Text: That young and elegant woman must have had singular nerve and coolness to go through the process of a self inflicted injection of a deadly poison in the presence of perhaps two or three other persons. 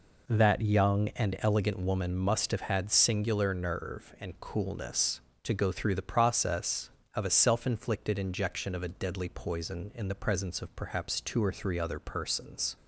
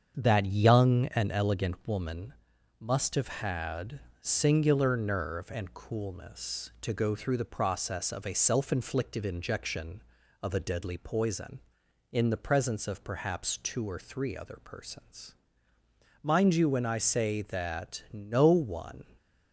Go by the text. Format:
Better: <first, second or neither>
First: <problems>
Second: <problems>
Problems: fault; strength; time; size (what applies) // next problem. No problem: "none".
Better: first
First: none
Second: starts louder than the rest; strong; until 1.1 s; 7.5 dB // pauses between "woman" and "must"; noticeable; at 2.3 s; 0.48 s long // pauses between "had" and "singular"; slight; at 3.9 s; 0.22 s long // goes on to say "Mind you when I say that no one"; strong; from 16.2 s on; 2.8 s long